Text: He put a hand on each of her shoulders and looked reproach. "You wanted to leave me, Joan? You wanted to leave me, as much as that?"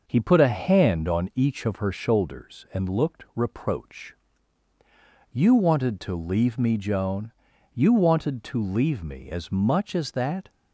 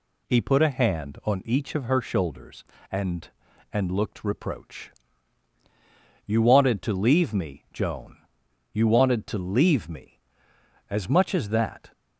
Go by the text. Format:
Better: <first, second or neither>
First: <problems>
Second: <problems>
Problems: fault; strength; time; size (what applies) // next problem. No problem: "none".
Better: first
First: none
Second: says "and" twice; at 3.7 s